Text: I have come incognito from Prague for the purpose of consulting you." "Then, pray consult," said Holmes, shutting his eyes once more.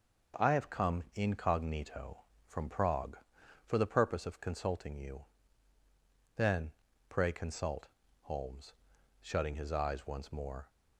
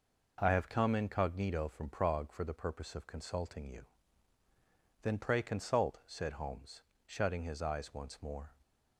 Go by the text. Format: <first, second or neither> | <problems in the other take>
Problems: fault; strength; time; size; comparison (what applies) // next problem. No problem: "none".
second | skips "said"; at 8.0 s